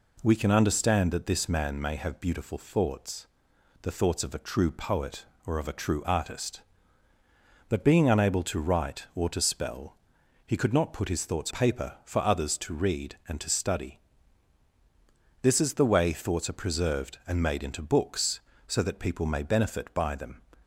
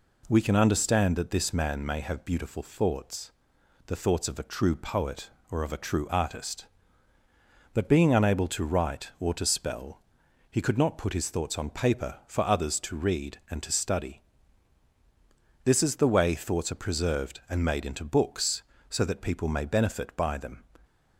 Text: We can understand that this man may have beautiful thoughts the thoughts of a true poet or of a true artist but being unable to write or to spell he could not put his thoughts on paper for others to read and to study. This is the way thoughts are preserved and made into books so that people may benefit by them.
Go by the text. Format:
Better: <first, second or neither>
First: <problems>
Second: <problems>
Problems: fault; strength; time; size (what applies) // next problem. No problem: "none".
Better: second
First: pauses between "thoughts" and "the"; noticeable; at 3.2 s; 0.56 s long // pauses between "spell" and "he"; noticeable; at 9.9 s; 0.50 s long // skips "on"; at 11.5 s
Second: pauses between "thoughts" and "the"; noticeable; at 3.3 s; 0.56 s long // pauses between "spell" and "he"; noticeable; at 9.9 s; 0.50 s long